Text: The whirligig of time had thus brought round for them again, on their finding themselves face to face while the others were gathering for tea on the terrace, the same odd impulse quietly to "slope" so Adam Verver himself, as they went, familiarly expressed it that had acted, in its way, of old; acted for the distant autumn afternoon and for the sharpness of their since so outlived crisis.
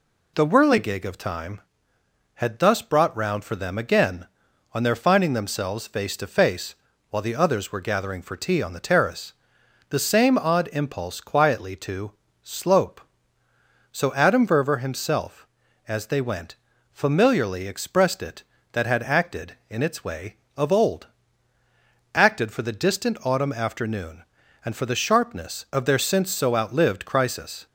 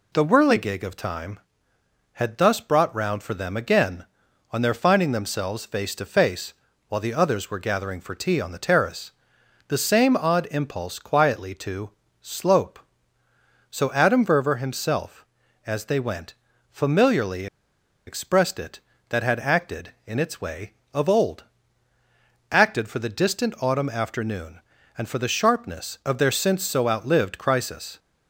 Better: first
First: pauses between "face" and "while"; slight; at 6.7 s; 0.36 s long // pauses between "to" and "slope"; slight; at 12.1 s; 0.28 s long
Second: pauses between "face" and "while"; slight; at 6.5 s; 0.36 s long // pauses between "to" and "slope"; slight; at 11.9 s; 0.28 s long // pauses between "familiarly" and "expressed"; noticeable; at 17.4 s; 0.60 s long

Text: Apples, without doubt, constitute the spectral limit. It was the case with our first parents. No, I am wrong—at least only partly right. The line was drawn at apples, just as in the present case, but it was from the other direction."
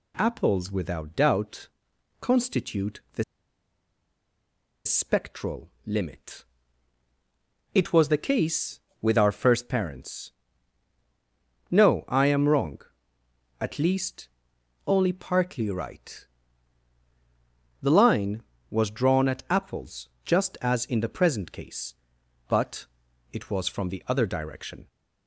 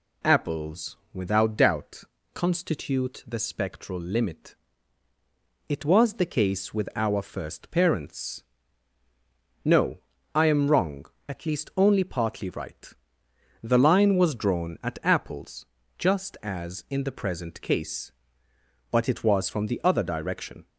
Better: second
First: pauses between "the" and "spectral"; strong; at 3.2 s; 1.6 s long // pauses between "spectral" and "limit"; slight; at 5.6 s; 0.16 s long // pauses between "least" and "only"; noticeable; at 14.2 s; 0.60 s long // pauses between "but" and "it"; noticeable; at 22.8 s; 0.48 s long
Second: none

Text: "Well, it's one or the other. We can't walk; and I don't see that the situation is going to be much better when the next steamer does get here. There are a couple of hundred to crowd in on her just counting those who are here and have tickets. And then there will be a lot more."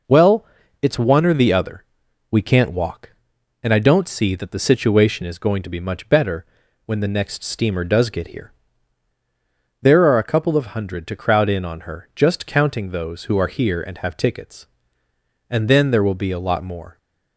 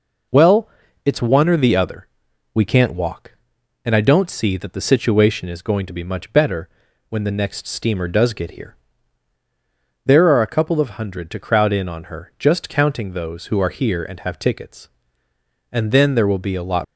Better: first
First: pauses between "better" and "when"; at 6.4 s; 0.40 s long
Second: pauses between "better" and "when"; at 6.6 s; 0.40 s long // stops before "more"; at 16.8 s

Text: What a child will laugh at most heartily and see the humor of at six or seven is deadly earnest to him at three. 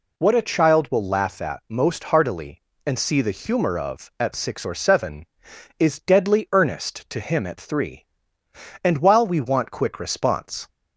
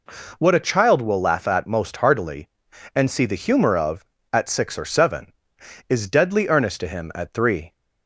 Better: second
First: goes on to say "And while we want quick response"; strong; from 8.8 s on; 1.8 s long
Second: none

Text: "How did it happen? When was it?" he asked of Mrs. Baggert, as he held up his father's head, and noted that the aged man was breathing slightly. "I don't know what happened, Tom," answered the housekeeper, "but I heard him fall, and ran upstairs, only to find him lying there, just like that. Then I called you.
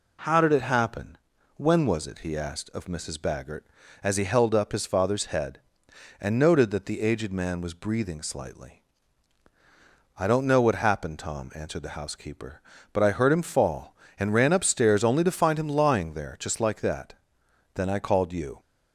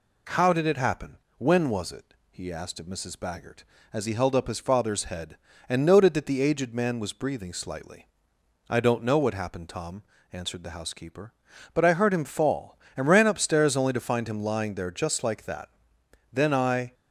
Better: first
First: none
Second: stops before "called you"; at 16.9 s

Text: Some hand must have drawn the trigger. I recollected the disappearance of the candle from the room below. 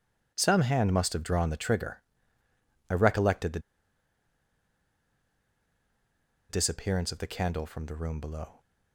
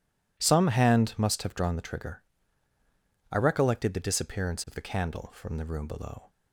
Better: second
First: pauses between "the" and "disappearance"; strong; at 3.5 s; 2.9 s long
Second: none

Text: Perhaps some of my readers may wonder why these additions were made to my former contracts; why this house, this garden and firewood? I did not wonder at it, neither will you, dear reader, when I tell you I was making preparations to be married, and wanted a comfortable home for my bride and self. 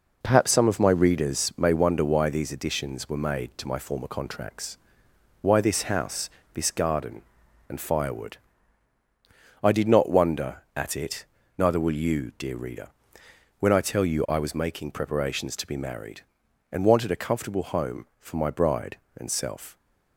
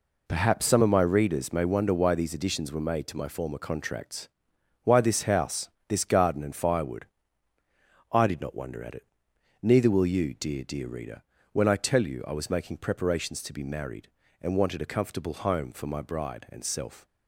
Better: first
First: none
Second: says "dear" twice; at 10.6 s

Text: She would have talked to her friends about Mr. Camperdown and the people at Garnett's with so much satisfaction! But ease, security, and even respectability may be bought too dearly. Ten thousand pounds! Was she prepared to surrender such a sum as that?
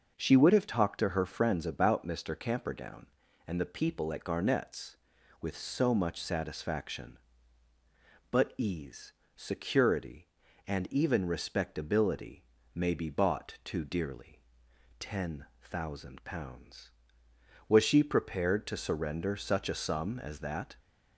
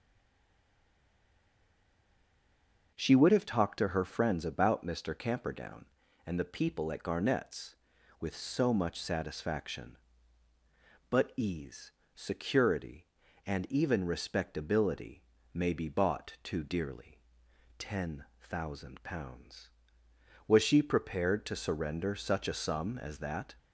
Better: first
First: starts louder than the rest; noticeable; until 1.1 s; 6 dB // pauses between "respectability" and "may"; slight; at 12.4 s; 0.30 s long // pauses between "Ten" and "thousand"; slight; at 15.4 s; 0.16 s long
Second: stays silent before the first word; strong; until 2.9 s; 2.9 s long // starts louder than the rest; noticeable; until 3.9 s; 6 dB // pauses between "respectability" and "may"; slight; at 15.2 s; 0.30 s long // pauses between "Ten" and "thousand"; slight; at 18.2 s; 0.16 s long

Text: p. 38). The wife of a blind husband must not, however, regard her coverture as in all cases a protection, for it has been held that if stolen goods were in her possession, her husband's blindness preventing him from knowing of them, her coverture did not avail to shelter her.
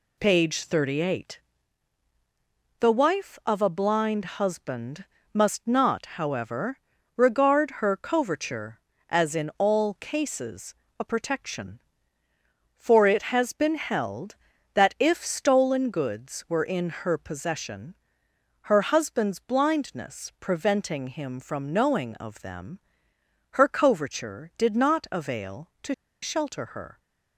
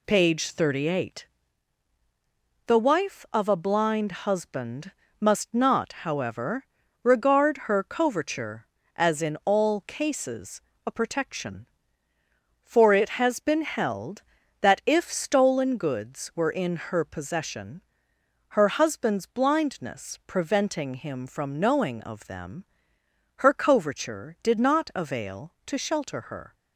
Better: second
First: pauses between "husband" and "must"; slight; at 5.0 s; 0.28 s long // pauses between "cases" and "a"; slight; at 10.7 s; 0.24 s long // pauses between "to" and "shelter"; slight; at 25.9 s; 0.28 s long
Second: pauses between "husband" and "must"; slight; at 4.9 s; 0.28 s long // pauses between "cases" and "a"; slight; at 10.6 s; 0.24 s long

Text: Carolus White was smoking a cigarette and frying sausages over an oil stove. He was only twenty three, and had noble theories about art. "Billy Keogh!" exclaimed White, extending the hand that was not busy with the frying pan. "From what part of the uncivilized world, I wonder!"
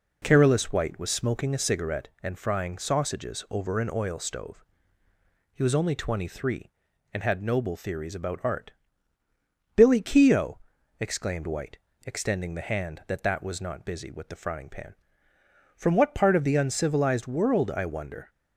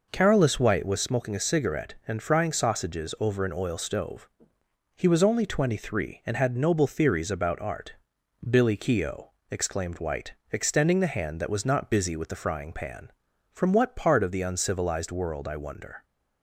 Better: second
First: says "that" twice; at 13.2 s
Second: none

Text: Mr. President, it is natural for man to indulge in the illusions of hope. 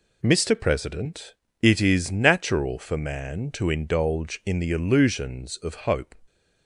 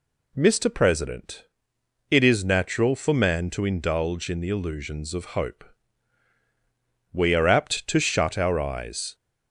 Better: first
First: none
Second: goes on to say "We are apt to shut our eyes"; strong; from 7.1 s on; 2.0 s long

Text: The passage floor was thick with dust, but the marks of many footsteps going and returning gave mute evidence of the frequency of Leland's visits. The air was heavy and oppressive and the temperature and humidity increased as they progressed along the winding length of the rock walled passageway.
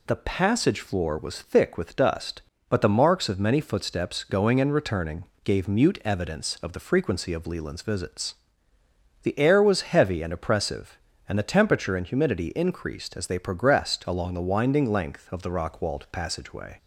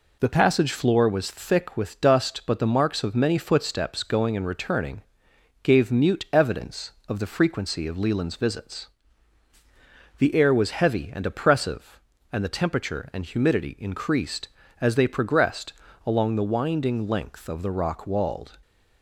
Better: first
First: pauses between "returning" and "gave"; slight; at 5.2 s; 0.20 s long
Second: pauses between "returning" and "gave"; noticeable; at 5.0 s; 0.60 s long // pauses between "progressed" and "along"; slight; at 15.7 s; 0.32 s long // stops before "passageway"; at 18.6 s

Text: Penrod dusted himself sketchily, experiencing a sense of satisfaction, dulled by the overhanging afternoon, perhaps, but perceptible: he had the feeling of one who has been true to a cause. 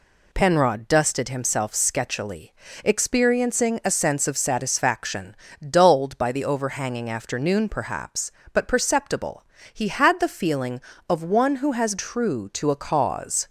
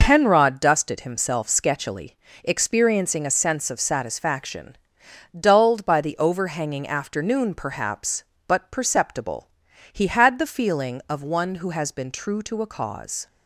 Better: second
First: skips "been"; at 11.9 s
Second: none

